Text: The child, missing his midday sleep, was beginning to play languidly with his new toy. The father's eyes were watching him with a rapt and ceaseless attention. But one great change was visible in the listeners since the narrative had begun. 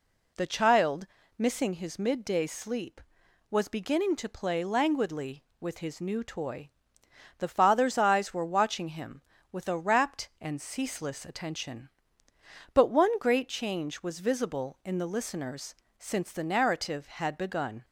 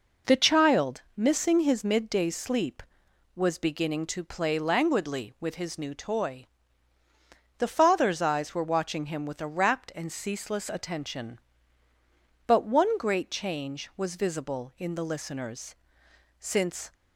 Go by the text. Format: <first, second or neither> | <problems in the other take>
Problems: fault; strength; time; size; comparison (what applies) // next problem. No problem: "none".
first | pauses between "listeners" and "since"; noticeable; at 15.7 s; 0.64 s long; slight in the first // stops before "the narrative had begun"; at 16.9 s